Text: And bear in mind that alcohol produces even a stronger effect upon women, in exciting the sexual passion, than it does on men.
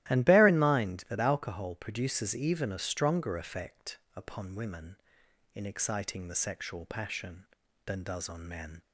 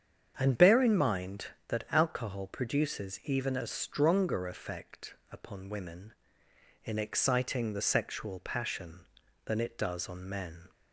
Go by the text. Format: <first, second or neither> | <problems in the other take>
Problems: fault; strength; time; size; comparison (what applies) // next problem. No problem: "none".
second | starts louder than the rest; strong; until 1.1 s; 15 dB; strong in the second // pauses between "effect" and "upon"; slight; at 3.9 s; 0.18 s long; slight in the second // skips "it"; at 8.0 s